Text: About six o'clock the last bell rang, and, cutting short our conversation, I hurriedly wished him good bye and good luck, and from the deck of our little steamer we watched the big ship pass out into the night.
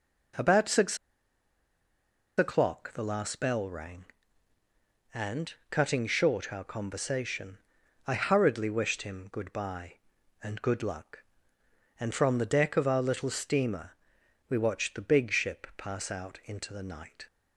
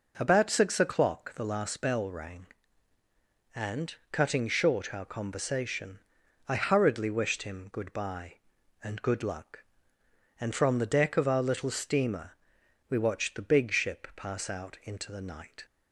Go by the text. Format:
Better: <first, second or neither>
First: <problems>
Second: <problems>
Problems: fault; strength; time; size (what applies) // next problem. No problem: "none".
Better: second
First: pauses between "six" and "o'clock"; strong; at 0.9 s; 1.4 s long // pauses between "steamer" and "we"; noticeable; at 13.9 s; 0.58 s long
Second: pauses between "steamer" and "we"; noticeable; at 12.3 s; 0.58 s long